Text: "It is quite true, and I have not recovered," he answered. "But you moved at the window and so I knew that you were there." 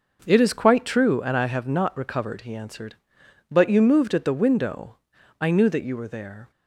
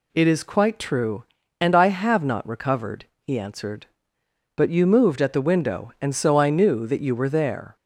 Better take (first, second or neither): second